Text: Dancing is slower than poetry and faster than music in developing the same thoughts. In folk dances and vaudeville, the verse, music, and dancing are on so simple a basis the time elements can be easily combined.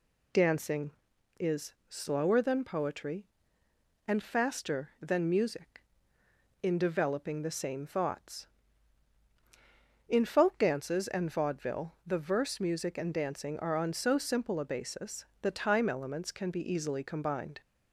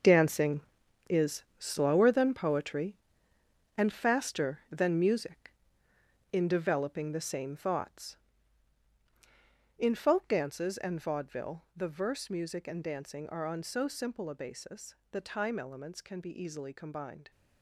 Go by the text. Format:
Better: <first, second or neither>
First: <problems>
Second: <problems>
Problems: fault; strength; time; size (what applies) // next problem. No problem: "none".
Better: first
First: pauses between "is" and "slower"; slight; at 1.7 s; 0.16 s long // pauses between "basis" and "the"; slight; at 15.2 s; 0.16 s long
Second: gets quieter; strong; throughout; 11.5 dB // pauses between "is" and "slower"; slight; at 1.4 s; 0.16 s long // pauses between "basis" and "the"; slight; at 14.9 s; 0.16 s long